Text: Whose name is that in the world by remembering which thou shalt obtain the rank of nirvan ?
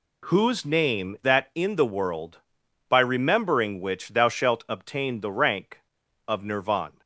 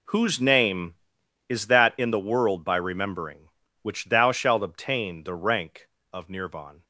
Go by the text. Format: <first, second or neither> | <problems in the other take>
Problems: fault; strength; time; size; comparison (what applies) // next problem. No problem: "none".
second | skips "is"; at 1.2 s